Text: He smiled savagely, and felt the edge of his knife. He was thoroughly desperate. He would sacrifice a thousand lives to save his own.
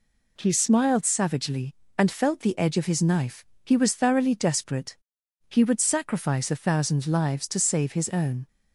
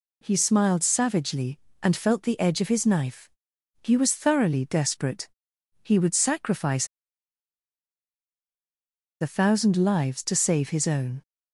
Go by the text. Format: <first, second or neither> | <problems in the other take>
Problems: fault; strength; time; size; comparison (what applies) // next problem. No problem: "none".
first | pauses between "sacrifice" and "a"; strong; at 6.8 s; 2.3 s long